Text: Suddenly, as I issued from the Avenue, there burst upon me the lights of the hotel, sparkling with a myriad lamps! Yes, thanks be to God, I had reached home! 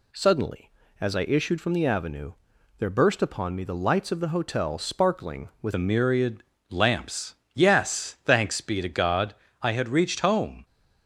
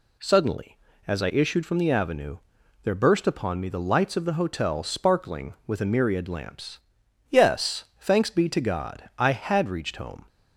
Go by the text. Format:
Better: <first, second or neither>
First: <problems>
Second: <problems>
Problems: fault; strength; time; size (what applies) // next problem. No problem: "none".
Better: second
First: changes voice at "a"; from 5.7 s on; 4.9 s long // pauses between "myriad" and "lamps"; slight; at 6.4 s; 0.26 s long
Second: none